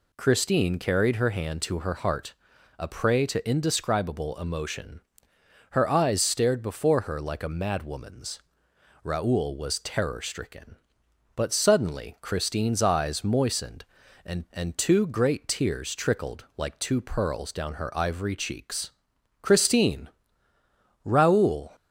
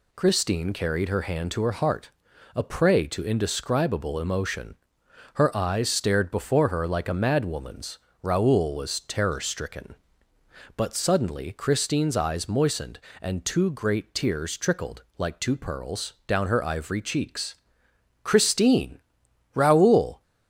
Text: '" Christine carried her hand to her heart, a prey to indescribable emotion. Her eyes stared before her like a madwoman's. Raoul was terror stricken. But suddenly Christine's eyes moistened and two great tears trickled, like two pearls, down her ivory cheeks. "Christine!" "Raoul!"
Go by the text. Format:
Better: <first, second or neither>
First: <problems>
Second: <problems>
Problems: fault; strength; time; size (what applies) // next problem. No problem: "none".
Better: second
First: says "and" twice; at 14.5 s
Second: none